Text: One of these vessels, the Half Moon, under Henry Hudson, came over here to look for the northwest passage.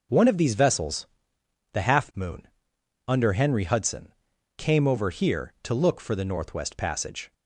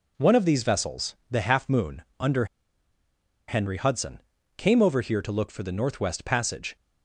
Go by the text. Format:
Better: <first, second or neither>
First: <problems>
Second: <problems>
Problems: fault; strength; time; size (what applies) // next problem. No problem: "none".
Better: first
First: none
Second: pauses between "under" and "Henry"; at 2.4 s; 1.0 s long